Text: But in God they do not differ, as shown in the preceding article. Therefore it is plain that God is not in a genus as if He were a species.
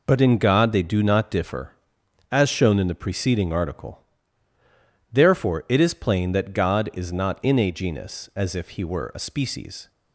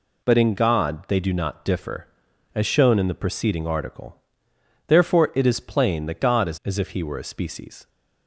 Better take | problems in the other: first | skips "not in a genus"; at 6.6 s

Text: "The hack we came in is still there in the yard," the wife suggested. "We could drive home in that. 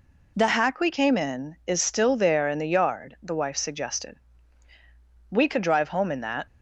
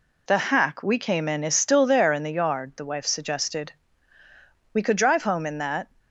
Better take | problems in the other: neither | none

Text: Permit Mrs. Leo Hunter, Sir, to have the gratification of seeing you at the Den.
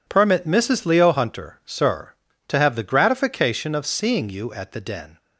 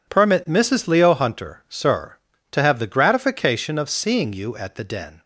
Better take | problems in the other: neither | none

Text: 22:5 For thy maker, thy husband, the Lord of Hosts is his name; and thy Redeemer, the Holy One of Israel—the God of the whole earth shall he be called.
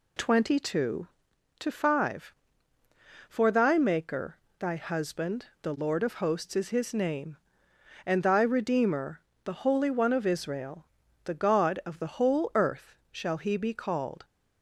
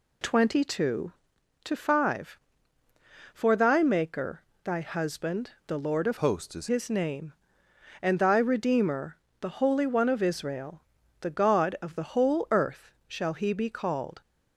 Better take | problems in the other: first | changes voice from "Hosts" to "is"; from 6.1 to 6.6 s; 0.5 s long // pauses between "earth" and "shall"; slight; at 12.9 s; 0.16 s long; slight in the first

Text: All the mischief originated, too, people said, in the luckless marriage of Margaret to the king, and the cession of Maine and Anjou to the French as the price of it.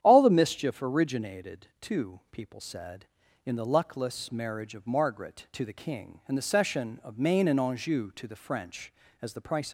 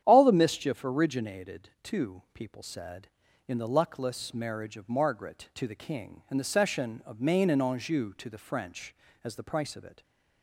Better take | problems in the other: second | starts louder than the rest; strong; until 1.0 s; 9.5 dB; strong in the second // stops before "of it"; at 9.6 s

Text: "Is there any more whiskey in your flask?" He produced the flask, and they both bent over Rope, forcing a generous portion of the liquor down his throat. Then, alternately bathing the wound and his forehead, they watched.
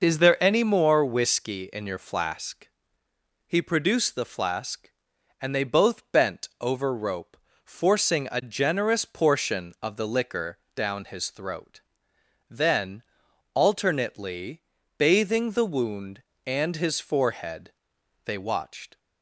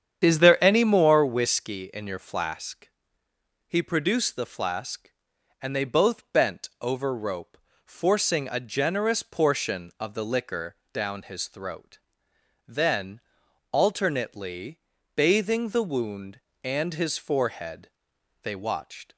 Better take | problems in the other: first | starts louder than the rest; strong; until 1.4 s; 8.5 dB // pauses between "liquor" and "down"; slight; at 10.7 s; 0.18 s long; slight in the first // pauses between "alternately" and "bathing"; slight; at 14.7 s; 0.36 s long; slight in the first

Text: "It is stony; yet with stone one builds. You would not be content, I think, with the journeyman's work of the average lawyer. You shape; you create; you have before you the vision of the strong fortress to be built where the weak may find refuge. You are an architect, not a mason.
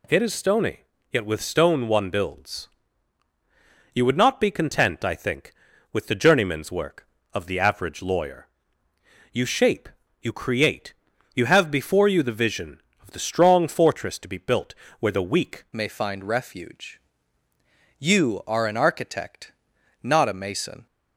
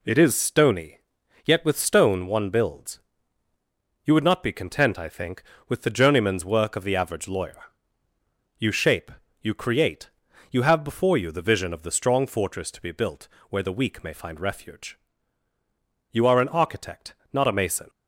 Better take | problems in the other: second | pauses between "built" and "where"; slight; at 14.7 s; 0.24 s long; slight in the second // changes voice at "may"; from 15.7 s on; 5.1 s long

